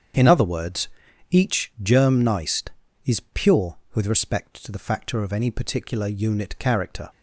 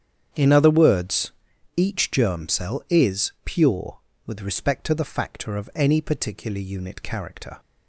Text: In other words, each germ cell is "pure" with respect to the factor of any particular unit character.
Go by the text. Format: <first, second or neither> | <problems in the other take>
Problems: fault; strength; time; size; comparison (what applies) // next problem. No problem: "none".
second | starts louder than the rest; strong; until 1.5 s; 8 dB; strong in the second // says "neist" for "cell"; at 2.2 s